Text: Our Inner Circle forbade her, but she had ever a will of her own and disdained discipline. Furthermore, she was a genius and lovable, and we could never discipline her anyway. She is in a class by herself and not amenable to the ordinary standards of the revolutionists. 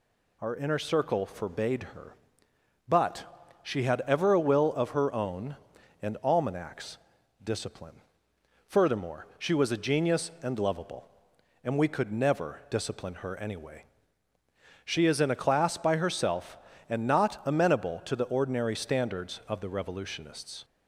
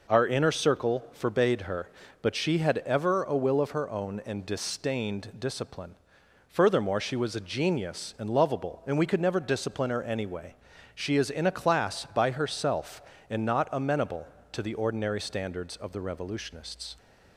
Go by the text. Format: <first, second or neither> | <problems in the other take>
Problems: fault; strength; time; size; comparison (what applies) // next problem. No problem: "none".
second | says "almanacs" for "disdained"; at 6.2 s